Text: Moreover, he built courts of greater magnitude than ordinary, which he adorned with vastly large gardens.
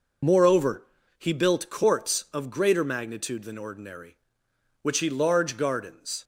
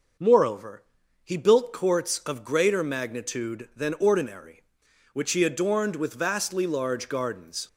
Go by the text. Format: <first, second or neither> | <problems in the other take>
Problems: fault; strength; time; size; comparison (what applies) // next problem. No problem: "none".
second | skips "adorned with vastly"; at 5.0 s